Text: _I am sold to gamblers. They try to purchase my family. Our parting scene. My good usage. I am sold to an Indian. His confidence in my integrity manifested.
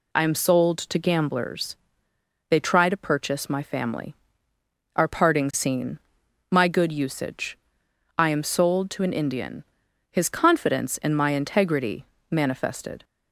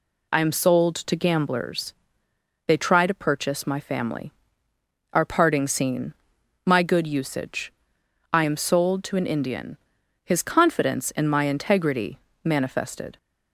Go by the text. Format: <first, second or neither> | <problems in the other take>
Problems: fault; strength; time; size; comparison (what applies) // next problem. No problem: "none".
neither | pauses between "integrity" and "manifested"; slight; the same in both